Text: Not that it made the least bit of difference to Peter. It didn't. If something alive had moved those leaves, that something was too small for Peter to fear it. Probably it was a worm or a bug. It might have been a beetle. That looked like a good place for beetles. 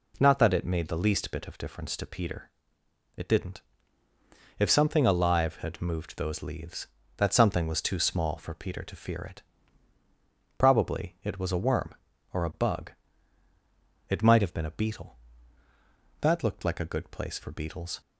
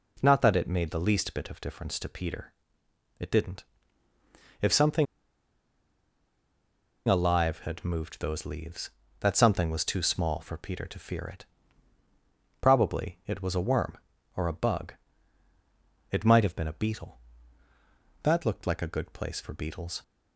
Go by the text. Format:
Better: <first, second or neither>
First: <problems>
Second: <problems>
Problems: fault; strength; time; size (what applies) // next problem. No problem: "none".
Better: first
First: none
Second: pauses between "something" and "alive"; strong; at 5.0 s; 2.0 s long